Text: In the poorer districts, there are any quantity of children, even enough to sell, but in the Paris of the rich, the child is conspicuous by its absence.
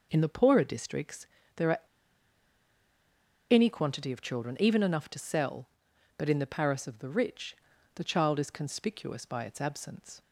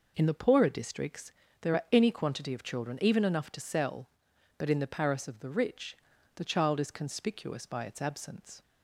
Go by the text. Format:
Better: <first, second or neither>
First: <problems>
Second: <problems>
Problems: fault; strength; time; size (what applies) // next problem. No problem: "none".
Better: second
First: pauses between "are" and "any"; strong; at 1.7 s; 1.7 s long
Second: none